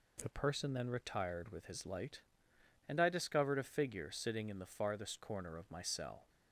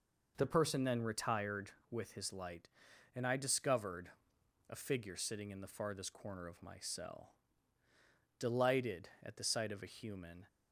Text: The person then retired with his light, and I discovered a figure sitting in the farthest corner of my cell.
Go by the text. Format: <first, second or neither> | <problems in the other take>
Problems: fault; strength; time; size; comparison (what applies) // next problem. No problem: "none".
first | pauses between "discovered" and "a"; noticeable; at 4.0 s; 0.58 s long // goes on to say "Delighted at the sight of a human"; strong; from 8.3 s on; 2.0 s long